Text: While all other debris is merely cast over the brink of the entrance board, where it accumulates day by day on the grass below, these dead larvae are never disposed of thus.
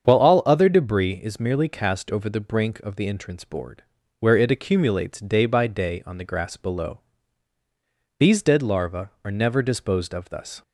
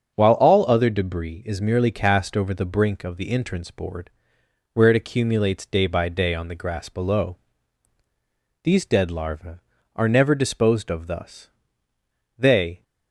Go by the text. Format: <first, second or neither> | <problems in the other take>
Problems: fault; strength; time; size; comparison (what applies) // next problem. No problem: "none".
first | starts louder than the rest; strong; until 1.1 s; 7 dB; strong in the first // goes on to say "They"; slight; from 12.3 s on; 0.46 s long